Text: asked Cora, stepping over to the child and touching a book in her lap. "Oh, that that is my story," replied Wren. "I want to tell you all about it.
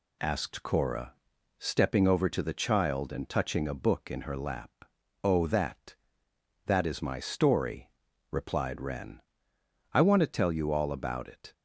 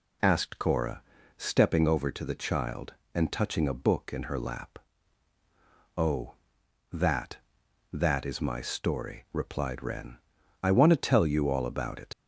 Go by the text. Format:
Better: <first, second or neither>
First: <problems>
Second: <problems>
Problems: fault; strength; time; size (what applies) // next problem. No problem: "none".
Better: first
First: none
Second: leaves "it" unfinished; at 12.1 s; 65 ms